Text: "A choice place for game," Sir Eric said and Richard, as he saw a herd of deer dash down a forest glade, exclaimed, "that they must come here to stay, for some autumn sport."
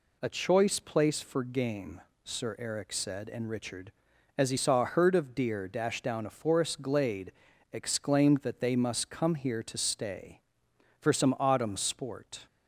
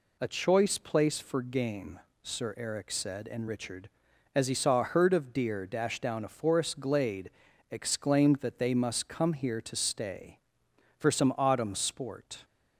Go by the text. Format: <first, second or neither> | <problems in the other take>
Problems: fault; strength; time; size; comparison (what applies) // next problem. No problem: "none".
neither | none